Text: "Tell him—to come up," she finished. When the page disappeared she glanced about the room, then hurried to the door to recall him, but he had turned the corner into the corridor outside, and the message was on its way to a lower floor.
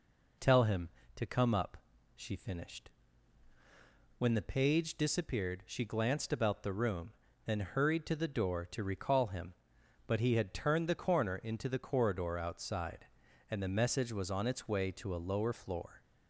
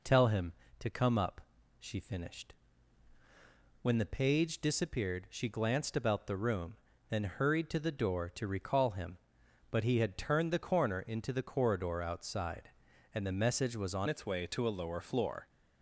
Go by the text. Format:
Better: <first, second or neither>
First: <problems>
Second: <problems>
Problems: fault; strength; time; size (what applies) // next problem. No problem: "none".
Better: first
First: none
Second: changes voice at "its"; from 14.0 s on; 1.4 s long